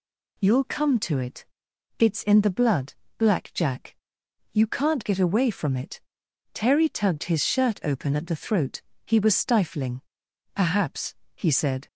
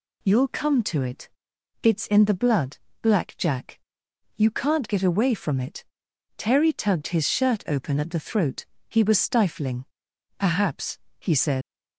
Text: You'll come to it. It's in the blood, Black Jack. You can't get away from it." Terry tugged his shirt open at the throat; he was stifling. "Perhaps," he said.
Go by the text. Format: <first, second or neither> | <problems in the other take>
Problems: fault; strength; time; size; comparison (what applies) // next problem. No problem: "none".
first | leaves "said" unfinished; at 11.6 s; 95 ms